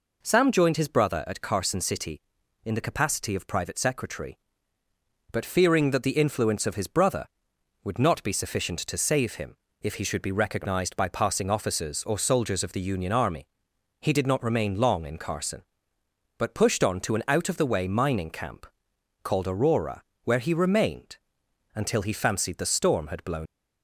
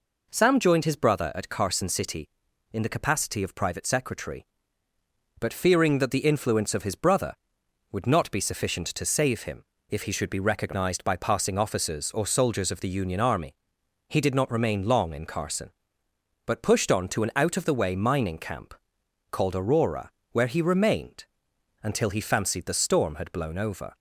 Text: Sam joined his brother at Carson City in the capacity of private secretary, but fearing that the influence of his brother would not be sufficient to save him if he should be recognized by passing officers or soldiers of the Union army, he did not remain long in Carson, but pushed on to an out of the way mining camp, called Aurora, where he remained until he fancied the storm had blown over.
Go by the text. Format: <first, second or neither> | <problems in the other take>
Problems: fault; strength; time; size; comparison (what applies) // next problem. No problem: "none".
second | pauses between "him" and "if"; slight; at 9.5 s; 0.26 s long; slight in the second // pauses between "remained" and "until"; noticeable; at 21.1 s; 0.58 s long; noticeable in the second // stops before "over"; at 23.4 s